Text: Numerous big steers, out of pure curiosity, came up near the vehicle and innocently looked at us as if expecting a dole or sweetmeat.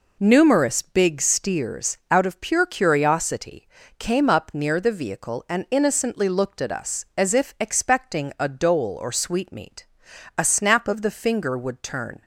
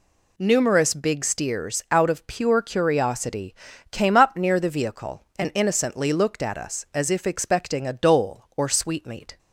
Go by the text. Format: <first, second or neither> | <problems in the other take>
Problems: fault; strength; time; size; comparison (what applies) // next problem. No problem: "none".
second | goes on to say "A snap of the finger would turn"; strong; from 10.3 s on; 1.8 s long